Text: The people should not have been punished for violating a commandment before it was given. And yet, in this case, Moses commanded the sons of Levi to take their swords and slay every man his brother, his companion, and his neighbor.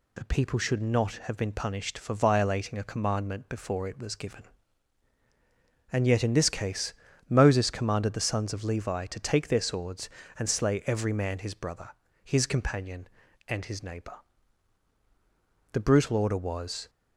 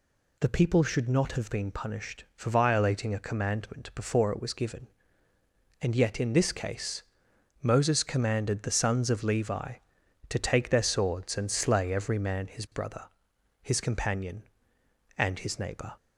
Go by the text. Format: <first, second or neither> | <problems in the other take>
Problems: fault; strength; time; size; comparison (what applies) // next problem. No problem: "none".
second | goes on to say "The brutal order was"; noticeable; from 15.7 s on; 1.1 s long